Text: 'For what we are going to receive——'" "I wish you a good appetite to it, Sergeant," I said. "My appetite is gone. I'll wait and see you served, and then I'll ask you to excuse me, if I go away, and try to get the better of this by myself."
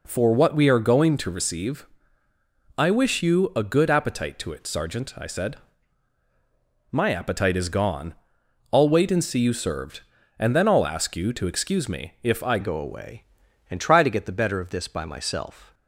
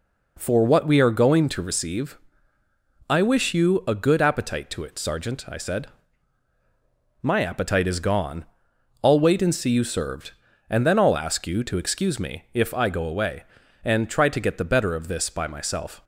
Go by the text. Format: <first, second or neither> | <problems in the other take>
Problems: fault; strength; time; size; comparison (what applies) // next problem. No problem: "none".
second | changes voice at "go"; from 12.6 s on; 3.1 s long